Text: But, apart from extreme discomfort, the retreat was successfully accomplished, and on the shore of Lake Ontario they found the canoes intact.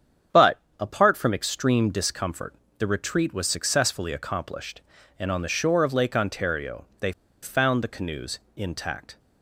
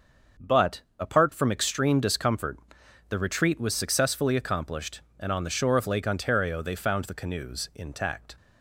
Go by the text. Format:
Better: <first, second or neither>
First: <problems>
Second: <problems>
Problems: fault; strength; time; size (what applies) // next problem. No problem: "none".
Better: second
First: starts louder than the rest; strong; until 1.5 s; 8 dB // pauses between "Ontario" and "they"; slight; at 6.8 s; 0.16 s long // pauses between "they" and "found"; slight; at 7.1 s; 0.30 s long // pauses between "canoes" and "intact"; slight; at 8.3 s; 0.18 s long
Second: starts louder than the rest; until 1.6 s; 6.5 dB